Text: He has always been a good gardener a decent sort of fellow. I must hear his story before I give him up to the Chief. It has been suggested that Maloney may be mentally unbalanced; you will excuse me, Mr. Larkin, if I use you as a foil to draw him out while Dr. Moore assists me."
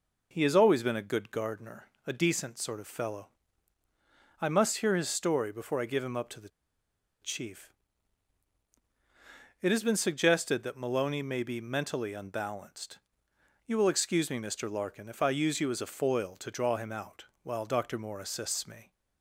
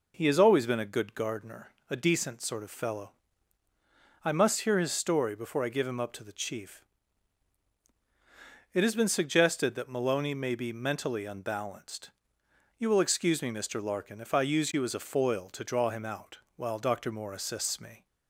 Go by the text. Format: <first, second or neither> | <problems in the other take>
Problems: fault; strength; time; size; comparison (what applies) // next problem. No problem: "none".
second | pauses between "gardener" and "a"; slight; at 1.8 s; 0.18 s long; slight in the second // pauses between "the" and "Chief"; noticeable; at 6.4 s; 0.73 s long // pauses between "out" and "while"; slight; at 17.2 s; 0.18 s long; slight in the second